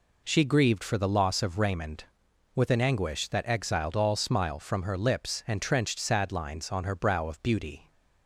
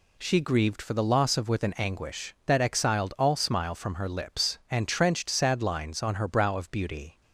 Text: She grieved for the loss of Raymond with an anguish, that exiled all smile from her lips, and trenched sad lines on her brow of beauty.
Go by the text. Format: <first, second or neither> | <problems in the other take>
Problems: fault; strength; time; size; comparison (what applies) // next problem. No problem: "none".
first | skips "Raymond"; at 1.4 s